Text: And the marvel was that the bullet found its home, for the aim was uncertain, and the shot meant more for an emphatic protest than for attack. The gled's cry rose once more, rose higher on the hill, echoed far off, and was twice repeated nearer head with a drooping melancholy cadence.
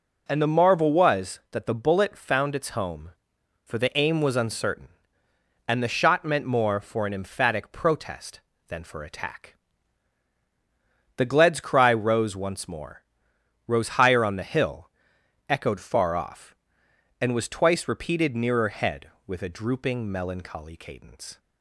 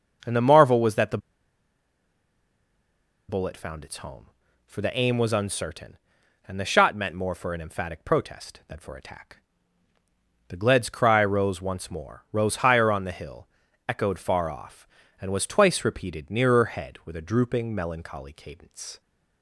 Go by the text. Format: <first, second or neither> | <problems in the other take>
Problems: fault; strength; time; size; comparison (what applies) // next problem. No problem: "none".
first | starts louder than the rest; noticeable; until 3.3 s; 6 dB // pauses between "the" and "bullet"; strong; at 1.1 s; 2.1 s long